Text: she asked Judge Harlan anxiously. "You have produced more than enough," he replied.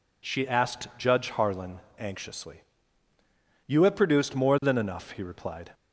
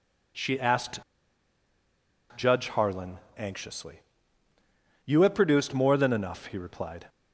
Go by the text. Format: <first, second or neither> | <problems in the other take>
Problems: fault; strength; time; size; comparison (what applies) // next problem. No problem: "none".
first | pauses between "asked" and "Judge"; strong; at 0.9 s; 1.3 s long // pauses between "Harlan" and "anxiously"; slight; at 3.1 s; 0.18 s long; slight in the first